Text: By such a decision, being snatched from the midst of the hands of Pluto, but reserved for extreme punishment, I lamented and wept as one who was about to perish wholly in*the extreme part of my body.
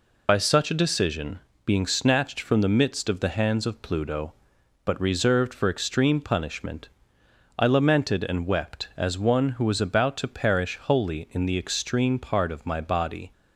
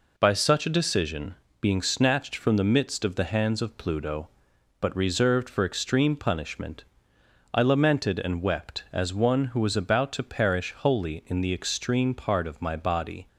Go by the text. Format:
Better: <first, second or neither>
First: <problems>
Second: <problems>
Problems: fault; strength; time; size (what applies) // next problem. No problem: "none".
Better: second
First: loses the start of "By"; at 0.2 s; 60 ms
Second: none